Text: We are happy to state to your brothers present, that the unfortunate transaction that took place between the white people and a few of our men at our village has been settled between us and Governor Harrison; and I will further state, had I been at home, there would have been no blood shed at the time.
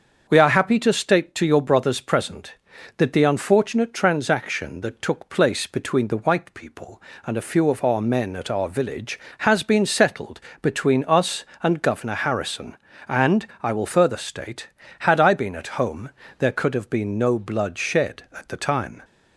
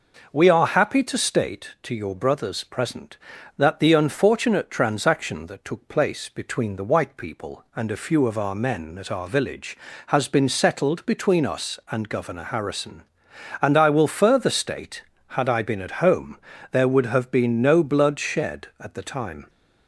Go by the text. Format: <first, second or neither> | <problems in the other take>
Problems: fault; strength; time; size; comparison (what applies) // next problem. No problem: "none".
second | starts louder than the rest; until 1.3 s; 6.5 dB // pauses between "settled" and "between"; slight; at 10.4 s; 0.20 s long // pauses between "and" and "I"; slight; at 13.4 s; 0.16 s long // says "could" for "would"; at 16.5 s